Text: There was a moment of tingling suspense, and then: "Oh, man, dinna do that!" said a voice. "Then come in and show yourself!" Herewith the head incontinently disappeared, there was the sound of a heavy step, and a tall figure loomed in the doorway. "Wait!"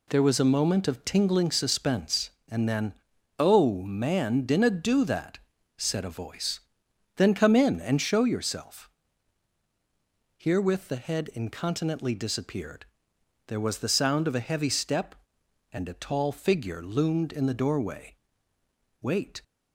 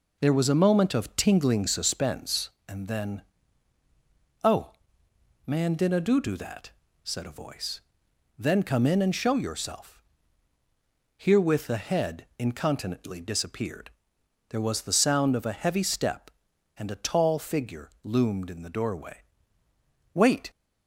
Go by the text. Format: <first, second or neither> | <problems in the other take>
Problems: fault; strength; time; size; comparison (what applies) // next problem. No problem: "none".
first | says "do" twice; at 6.1 s